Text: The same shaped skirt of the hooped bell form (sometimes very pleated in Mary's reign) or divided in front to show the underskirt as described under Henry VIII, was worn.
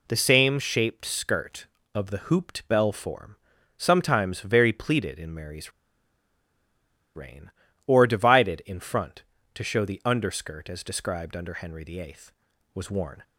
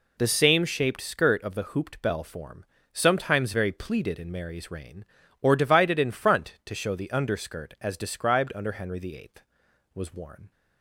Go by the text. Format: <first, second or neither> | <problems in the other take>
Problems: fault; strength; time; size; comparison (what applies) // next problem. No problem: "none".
second | pauses between "Mary's" and "reign"; strong; at 5.7 s; 1.4 s long